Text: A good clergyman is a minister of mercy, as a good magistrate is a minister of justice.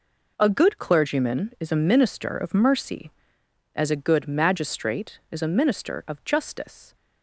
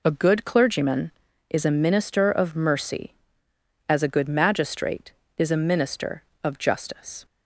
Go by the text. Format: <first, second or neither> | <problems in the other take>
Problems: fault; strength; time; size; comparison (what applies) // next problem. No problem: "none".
neither | none